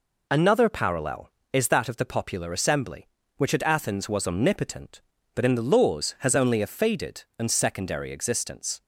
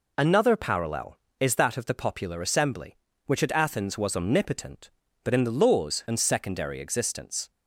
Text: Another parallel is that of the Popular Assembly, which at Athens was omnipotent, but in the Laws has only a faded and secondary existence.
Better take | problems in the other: first | skips "has only a faded"; at 6.0 s

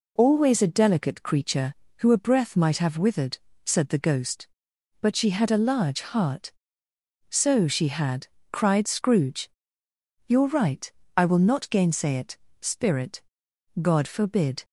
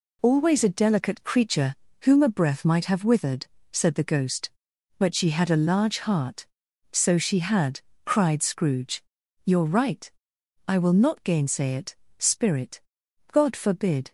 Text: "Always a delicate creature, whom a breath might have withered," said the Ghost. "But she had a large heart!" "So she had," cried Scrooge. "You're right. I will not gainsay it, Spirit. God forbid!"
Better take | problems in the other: second | says "who" for "whom"; at 1.9 s

